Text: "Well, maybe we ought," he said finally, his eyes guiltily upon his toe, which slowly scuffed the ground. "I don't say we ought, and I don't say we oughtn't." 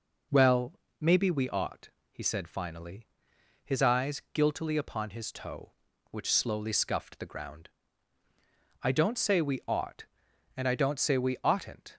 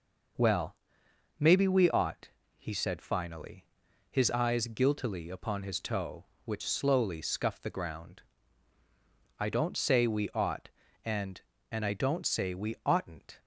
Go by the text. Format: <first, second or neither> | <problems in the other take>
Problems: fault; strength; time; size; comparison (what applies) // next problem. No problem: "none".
first | says "and" twice; at 11.7 s